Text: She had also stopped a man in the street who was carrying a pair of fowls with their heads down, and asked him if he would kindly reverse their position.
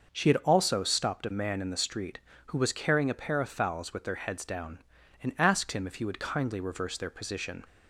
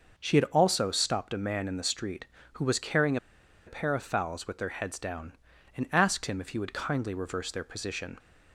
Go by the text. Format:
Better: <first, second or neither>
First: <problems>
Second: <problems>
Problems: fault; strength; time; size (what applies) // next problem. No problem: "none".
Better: first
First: starts louder than the rest; noticeable; until 1.1 s; 6 dB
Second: starts louder than the rest; noticeable; until 1.1 s; 6 dB // pauses between "carrying" and "a"; noticeable; at 3.1 s; 0.50 s long